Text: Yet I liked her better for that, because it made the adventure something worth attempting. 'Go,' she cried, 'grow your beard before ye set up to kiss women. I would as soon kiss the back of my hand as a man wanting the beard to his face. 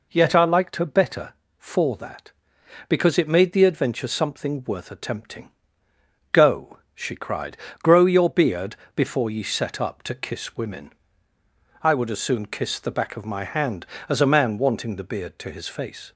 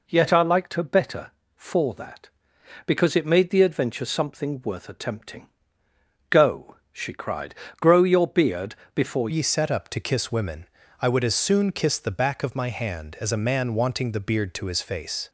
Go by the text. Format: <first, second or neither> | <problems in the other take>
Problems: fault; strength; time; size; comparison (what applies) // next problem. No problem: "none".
first | pauses between "beard" and "before"; slight; at 8.7 s; 0.20 s long; slight in the first // changes voice at "ye"; from 9.2 s on; 6.0 s long